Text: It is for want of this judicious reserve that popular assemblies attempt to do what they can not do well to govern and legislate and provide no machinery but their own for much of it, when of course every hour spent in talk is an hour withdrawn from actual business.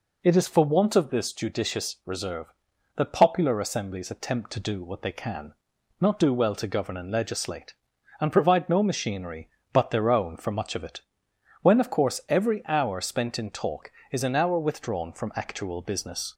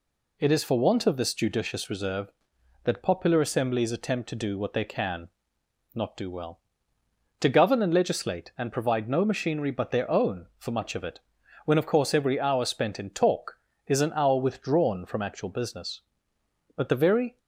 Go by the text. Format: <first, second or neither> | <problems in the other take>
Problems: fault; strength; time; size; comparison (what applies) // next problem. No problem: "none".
first | pauses between "can" and "not"; noticeable; at 5.2 s; 0.66 s long; noticeable in the first // goes on to say "But the very"; noticeable; from 16.7 s on; 0.62 s long